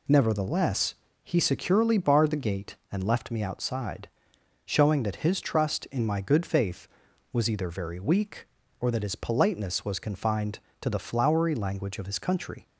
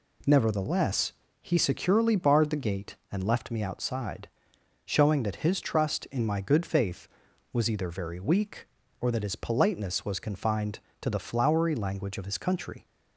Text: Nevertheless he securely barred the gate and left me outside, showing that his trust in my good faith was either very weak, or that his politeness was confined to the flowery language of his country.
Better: second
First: loses the start of "Nevertheless"; at 0.0 s; 40 ms // pauses between "Nevertheless" and "he"; slight; at 0.9 s; 0.30 s long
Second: pauses between "Nevertheless" and "he"; slight; at 1.1 s; 0.30 s long

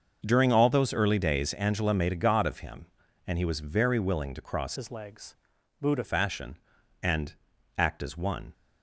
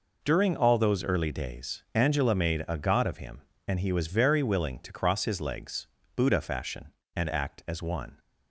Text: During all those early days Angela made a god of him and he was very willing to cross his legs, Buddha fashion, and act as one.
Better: second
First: starts louder than the rest; until 1.2 s; 6 dB // changes voice from "his" to "Buddha"; from 4.7 to 6.0 s; 1.3 s long // pauses between "and" and "act"; at 7.3 s; 0.42 s long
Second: none

